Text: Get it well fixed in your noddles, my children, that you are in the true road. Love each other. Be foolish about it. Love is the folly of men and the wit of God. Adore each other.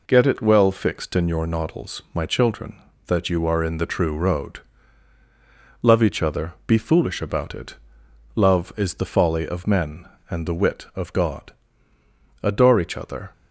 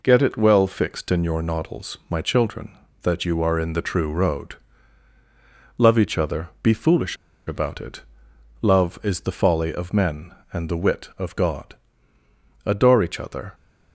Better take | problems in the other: first | pauses between "foolish" and "about"; slight; at 7.1 s; 0.31 s long

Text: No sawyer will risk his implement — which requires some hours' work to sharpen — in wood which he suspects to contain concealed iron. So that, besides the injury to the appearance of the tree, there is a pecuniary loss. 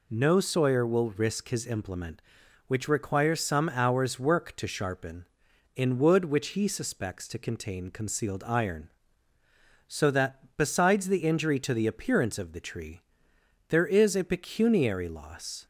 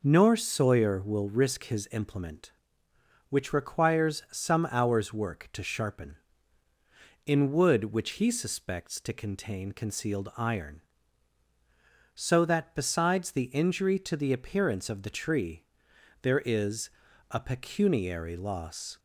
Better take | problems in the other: first | says "Nor" for "No"; at 0.0 s // pauses between "is" and "a"; at 16.8 s; 0.42 s long

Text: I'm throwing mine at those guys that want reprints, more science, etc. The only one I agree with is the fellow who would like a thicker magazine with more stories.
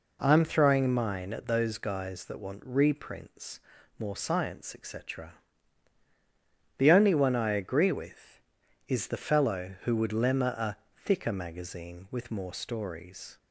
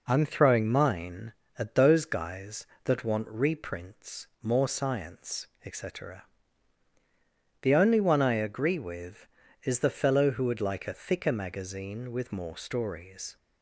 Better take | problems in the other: second | says "lemma" for "like"; at 10.1 s // pauses between "a" and "thicker"; slight; at 10.7 s; 0.18 s long

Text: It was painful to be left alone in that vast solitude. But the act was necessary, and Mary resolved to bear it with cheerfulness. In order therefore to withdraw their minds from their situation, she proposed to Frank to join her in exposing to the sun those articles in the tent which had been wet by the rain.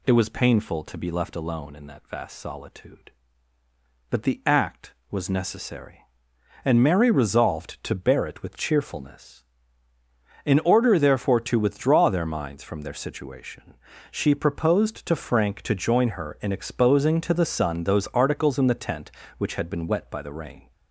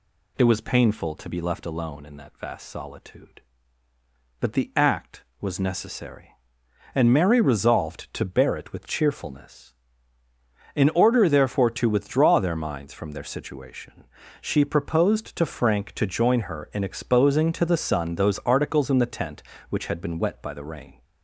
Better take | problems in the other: neither | none

